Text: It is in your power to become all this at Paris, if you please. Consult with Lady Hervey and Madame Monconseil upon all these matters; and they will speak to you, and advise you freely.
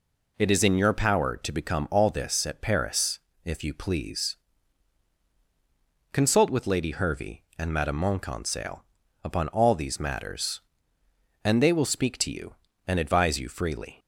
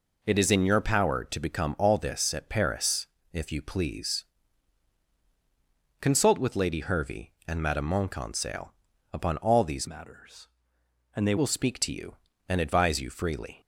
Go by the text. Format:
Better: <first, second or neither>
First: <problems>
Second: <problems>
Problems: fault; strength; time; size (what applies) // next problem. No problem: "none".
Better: first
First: pauses between "Monconseil" and "upon"; at 8.8 s; 0.40 s long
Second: pauses between "Monconseil" and "upon"; at 8.7 s; 0.40 s long // changes voice from "matters" to "they"; from 9.8 to 11.3 s; 1.5 s long